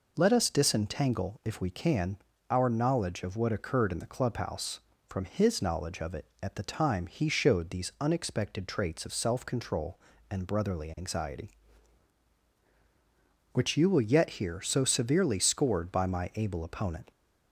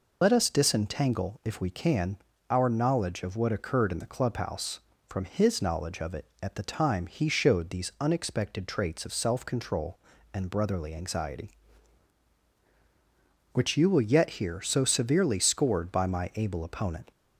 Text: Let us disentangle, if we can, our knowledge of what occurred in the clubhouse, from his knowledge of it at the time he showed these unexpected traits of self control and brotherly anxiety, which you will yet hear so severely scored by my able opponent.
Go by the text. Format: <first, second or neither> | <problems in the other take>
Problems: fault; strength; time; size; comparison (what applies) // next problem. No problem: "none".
first | loses the start of "Let"; at 0.2 s; 50 ms